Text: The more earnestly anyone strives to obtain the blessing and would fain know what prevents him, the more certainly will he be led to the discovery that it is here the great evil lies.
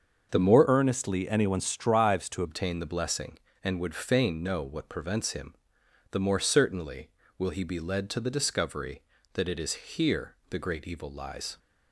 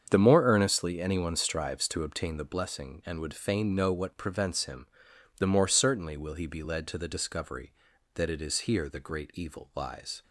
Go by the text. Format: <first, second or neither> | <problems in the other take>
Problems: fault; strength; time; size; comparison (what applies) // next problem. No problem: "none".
second | starts louder than the rest; until 1.3 s; 6.5 dB; strong in the second // changes voice from "earnestly" to "to"; from 0.6 to 2.4 s; 1.8 s long // pauses between "here" and "the"; slight; at 10.3 s; 0.16 s long